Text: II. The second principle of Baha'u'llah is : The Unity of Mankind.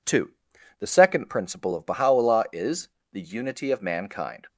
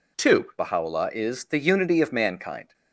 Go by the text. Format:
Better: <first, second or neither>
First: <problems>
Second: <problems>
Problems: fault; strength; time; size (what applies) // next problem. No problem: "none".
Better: first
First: none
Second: skips "The second principle of"; at 0.5 s